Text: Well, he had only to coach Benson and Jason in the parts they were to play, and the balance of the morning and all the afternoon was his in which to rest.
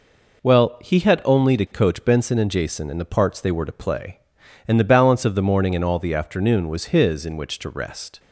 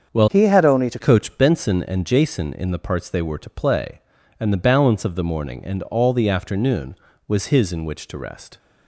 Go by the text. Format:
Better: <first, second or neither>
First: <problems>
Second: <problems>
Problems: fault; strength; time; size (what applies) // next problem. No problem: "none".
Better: first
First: none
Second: starts louder than the rest; until 1.1 s; 7 dB // changes voice from "he" to "to"; from 0.2 to 0.9 s; 0.7 s long